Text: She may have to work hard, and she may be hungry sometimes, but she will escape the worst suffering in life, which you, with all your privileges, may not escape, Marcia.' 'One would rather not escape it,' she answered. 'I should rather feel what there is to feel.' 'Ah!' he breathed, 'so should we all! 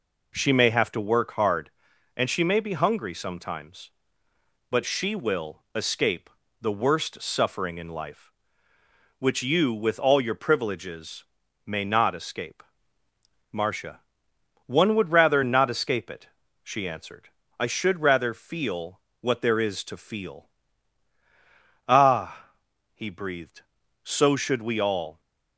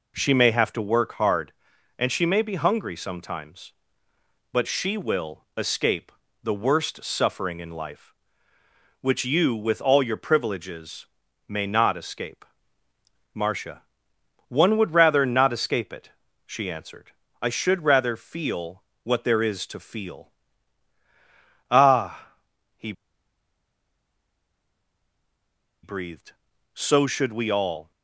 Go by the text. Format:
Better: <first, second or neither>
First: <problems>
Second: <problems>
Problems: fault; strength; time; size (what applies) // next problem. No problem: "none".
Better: first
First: pauses between "escape" and "the"; slight; at 6.2 s; 0.32 s long // pauses between "feel" and "what"; slight; at 19.0 s; 0.20 s long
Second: pauses between "escape" and "the"; slight; at 6.0 s; 0.32 s long // pauses between "feel" and "what"; slight; at 18.8 s; 0.20 s long // pauses between "he" and "breathed"; strong; at 22.9 s; 2.9 s long